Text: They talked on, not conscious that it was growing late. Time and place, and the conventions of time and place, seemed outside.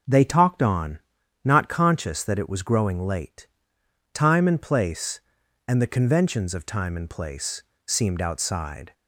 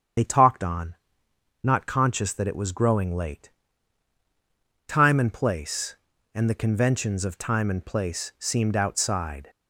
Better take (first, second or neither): first